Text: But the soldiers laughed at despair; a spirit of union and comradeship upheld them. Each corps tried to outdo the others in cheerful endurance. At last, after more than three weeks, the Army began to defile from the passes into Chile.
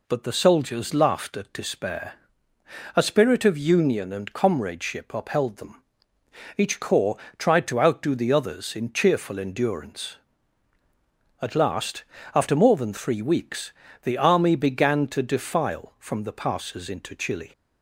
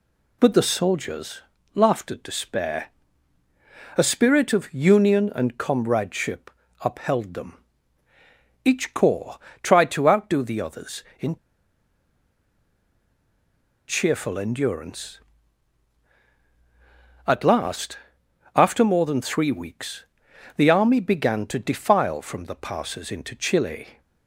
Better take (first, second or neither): first